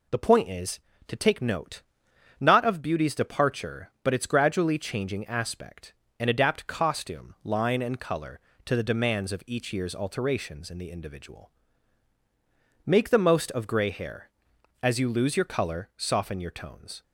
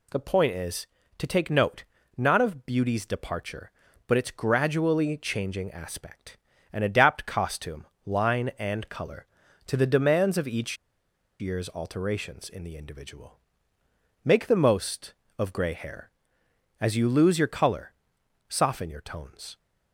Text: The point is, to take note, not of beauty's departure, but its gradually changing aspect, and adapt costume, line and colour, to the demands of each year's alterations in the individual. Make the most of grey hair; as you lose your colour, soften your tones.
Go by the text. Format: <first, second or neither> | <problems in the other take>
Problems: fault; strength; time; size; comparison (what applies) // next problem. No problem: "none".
first | pauses between "each" and "year's"; noticeable; at 10.7 s; 0.64 s long